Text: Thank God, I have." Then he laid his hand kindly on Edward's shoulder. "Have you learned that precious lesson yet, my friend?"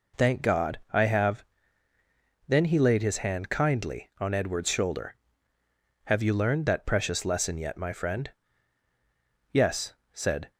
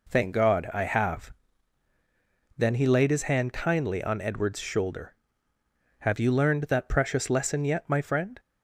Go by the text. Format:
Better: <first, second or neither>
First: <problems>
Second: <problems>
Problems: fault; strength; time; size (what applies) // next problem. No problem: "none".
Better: second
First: goes on to say "Yes said"; noticeable; from 9.5 s on; 1.0 s long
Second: none